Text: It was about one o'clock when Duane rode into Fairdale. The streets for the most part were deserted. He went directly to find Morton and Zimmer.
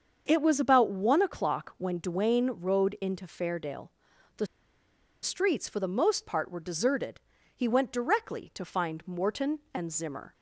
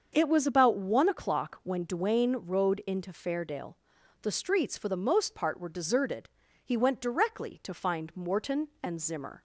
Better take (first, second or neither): second